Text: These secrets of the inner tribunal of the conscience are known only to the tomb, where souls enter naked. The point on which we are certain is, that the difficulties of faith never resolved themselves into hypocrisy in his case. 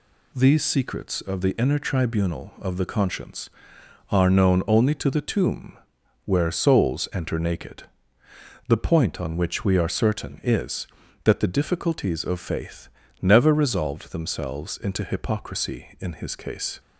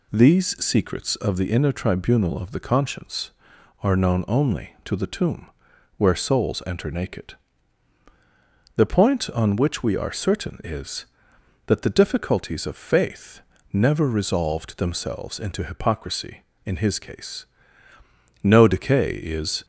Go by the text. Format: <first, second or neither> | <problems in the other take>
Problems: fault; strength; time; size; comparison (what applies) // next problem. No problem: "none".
first | pauses between "faith" and "never"; slight; at 13.4 s; 0.30 s long; slight in the first // goes on to say "No decay is"; noticeable; from 18.4 s on; 1.2 s long